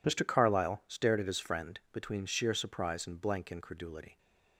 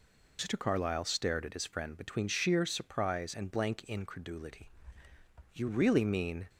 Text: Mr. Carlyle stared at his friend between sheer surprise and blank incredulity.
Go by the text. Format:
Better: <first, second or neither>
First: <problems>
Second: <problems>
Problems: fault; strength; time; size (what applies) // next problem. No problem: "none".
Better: first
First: none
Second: goes on to say "You really mean"; noticeable; from 5.5 s on; 0.96 s long